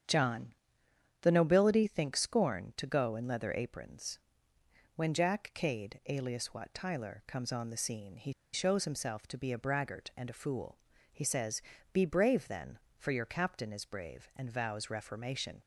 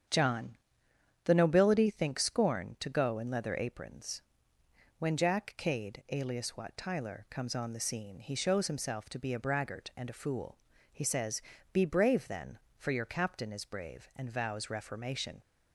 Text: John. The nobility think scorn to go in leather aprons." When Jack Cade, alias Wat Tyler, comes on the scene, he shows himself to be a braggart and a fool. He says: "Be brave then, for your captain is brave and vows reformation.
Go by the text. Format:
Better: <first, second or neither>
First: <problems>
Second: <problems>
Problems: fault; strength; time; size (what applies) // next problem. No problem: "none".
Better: second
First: starts louder than the rest; strong; until 1.7 s; 8.5 dB // pauses between "he" and "shows"; slight; at 8.3 s; 0.22 s long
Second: starts louder than the rest; strong; until 1.8 s; 8.5 dB